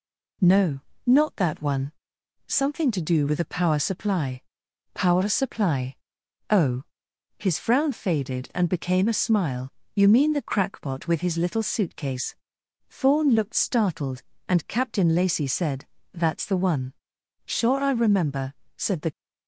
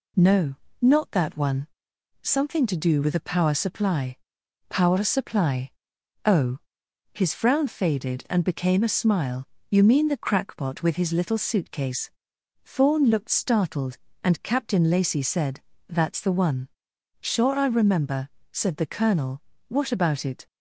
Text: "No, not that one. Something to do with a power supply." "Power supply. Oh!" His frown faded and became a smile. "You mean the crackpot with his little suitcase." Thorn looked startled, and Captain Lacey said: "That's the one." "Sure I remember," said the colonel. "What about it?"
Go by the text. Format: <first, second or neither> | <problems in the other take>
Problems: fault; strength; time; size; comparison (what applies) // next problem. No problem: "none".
second | stops before "colonel What about it"; at 19.1 s